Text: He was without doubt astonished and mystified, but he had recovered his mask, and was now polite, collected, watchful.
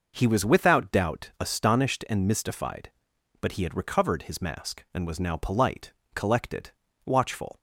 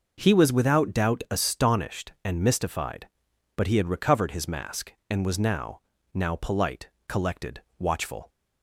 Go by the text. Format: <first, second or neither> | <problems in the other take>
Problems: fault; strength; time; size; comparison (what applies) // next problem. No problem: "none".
first | says "now" twice; at 6.1 s